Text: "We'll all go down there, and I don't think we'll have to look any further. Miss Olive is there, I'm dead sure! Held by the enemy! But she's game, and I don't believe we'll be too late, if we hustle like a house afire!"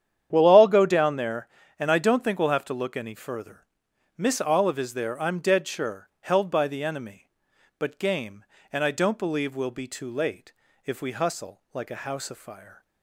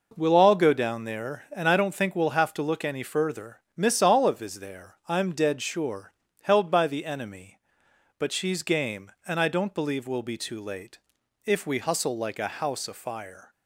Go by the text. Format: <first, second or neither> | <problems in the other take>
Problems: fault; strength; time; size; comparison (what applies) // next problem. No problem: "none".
second | starts louder than the rest; strong; until 1.3 s; 9.5 dB // skips "she's"; at 7.9 s